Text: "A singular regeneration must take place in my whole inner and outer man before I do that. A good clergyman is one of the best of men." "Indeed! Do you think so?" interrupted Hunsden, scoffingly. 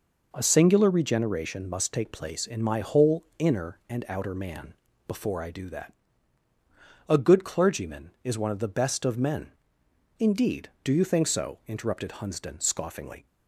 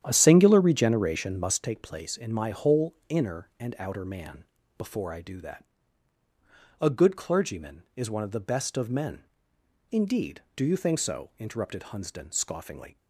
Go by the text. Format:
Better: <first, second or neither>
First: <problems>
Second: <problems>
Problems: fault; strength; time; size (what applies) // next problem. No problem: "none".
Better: first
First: pauses between "man" and "before"; slight; at 4.7 s; 0.30 s long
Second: starts louder than the rest; strong; until 1.6 s; 10 dB // pauses between "man" and "before"; slight; at 4.4 s; 0.30 s long